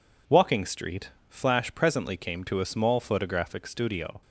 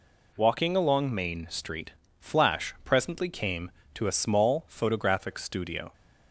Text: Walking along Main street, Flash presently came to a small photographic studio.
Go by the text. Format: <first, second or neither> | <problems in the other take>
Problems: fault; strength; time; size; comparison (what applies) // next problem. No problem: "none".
second | skips "along Main"; at 0.6 s